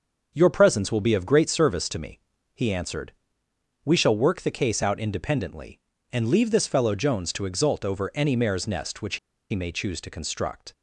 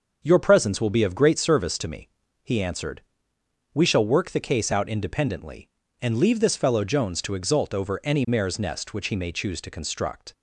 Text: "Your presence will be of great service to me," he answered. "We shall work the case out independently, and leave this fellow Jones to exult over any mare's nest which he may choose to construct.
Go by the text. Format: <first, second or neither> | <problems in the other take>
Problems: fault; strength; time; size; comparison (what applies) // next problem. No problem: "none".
second | starts louder than the rest; until 1.3 s; 6.5 dB; also in the second // pauses between "which" and "he"; slight; at 9.1 s; 0.33 s long